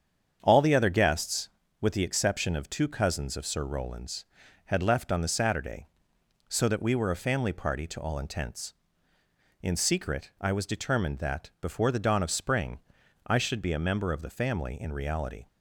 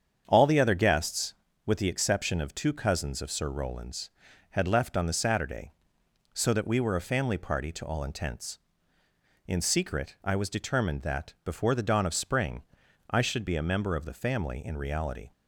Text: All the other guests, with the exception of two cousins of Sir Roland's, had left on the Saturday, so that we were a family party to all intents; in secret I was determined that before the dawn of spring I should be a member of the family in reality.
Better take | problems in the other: neither | starts louder than the rest; strong; the same in both // pauses between "spring" and "I"; noticeable; the same in both

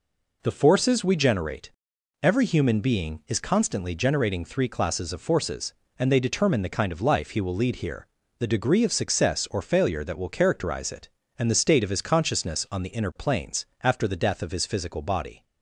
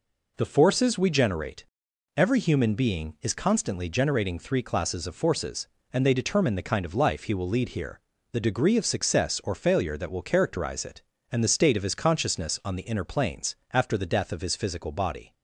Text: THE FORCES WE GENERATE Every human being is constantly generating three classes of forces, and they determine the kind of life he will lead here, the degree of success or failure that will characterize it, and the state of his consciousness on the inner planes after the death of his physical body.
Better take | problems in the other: neither | pauses between "GENERATE" and "Every"; noticeable; the same in both // pauses between "planes" and "after"; slight; the same in both

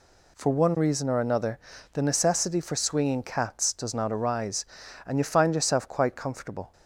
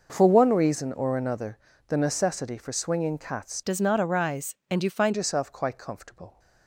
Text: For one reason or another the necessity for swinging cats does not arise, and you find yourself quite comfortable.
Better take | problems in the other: first | pauses between "another" and "the"; slight; at 1.5 s; 0.30 s long; slight in the first // changes voice from "does" to "find"; from 3.6 to 5.1 s; 1.5 s long

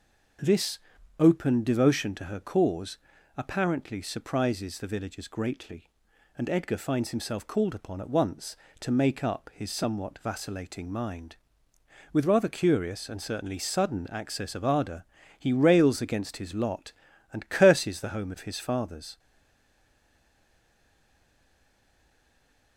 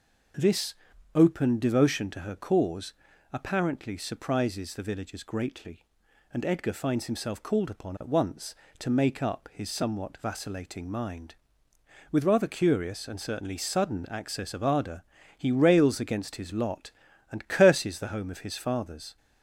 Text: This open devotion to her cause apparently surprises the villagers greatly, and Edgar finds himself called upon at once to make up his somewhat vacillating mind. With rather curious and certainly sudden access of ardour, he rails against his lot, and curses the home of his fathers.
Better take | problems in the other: second | pauses between "This" and "open"; at 0.7 s; 0.40 s long; also in the second // pauses between "cause" and "apparently"; at 2.9 s; 0.38 s long; also in the second // stays silent after the last word; strong; from 19.1 s on; 3.6 s long

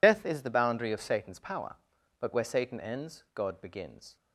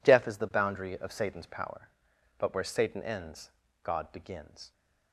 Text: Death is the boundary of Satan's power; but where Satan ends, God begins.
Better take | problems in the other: second | loses the start of "Death"; at 0.0 s; 65 ms

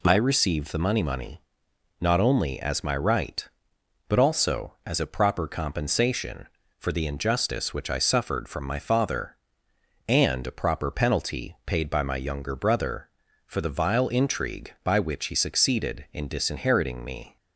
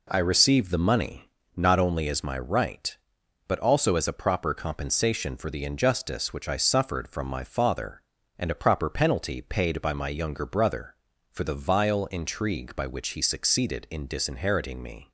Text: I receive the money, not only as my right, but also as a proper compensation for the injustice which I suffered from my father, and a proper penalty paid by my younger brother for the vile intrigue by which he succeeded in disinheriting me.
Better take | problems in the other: second | says "money" twice; at 1.0 s

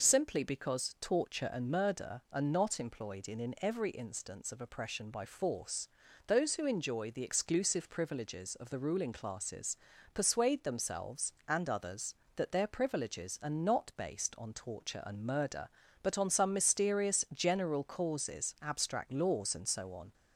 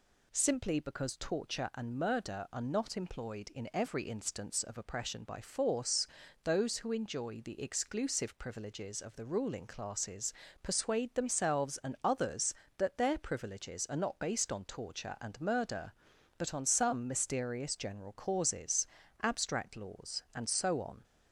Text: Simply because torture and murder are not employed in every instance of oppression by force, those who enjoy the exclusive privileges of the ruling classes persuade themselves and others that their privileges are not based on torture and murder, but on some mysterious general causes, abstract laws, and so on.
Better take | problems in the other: second | says "in" twice; at 3.3 s // pauses between "classes" and "persuade"; at 9.7 s; 0.38 s long; slight in the second

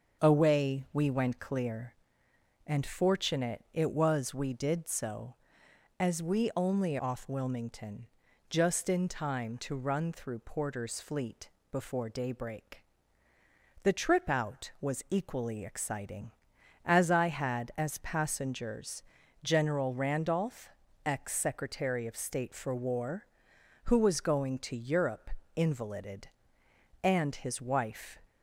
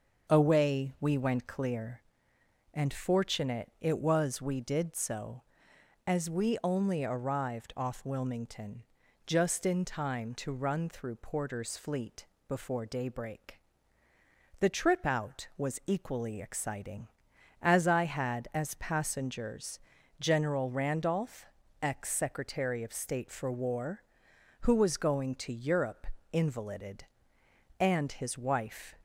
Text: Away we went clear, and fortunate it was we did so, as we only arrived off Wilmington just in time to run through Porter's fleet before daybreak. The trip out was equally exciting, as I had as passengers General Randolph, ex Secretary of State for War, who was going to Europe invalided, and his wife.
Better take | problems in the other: second | starts louder than the rest; until 1.2 s; 6.5 dB; also in the second // skips "arrived"; at 6.9 s // pauses between "Wilmington" and "just"; at 8.0 s; 0.42 s long; also in the second // pauses between "fleet" and "before"; slight; at 11.4 s; 0.22 s long; slight in the second // pauses between "passengers" and "General"; at 19.0 s; 0.40 s long; also in the second // pauses between "Europe" and "invalided"; slight; at 25.3 s; 0.24 s long; slight in the second

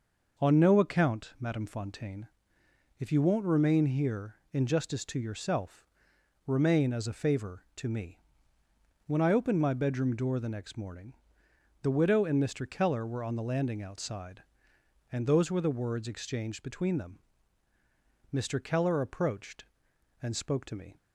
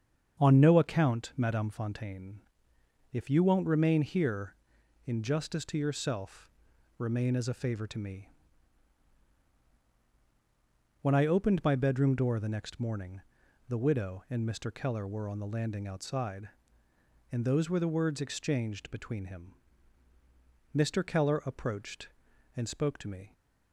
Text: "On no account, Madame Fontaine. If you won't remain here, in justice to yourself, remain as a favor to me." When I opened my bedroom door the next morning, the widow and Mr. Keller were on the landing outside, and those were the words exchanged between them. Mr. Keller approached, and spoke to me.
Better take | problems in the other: first | starts louder than the rest; strong; until 1.4 s; 7 dB // says "him" for "them"; at 19.2 s

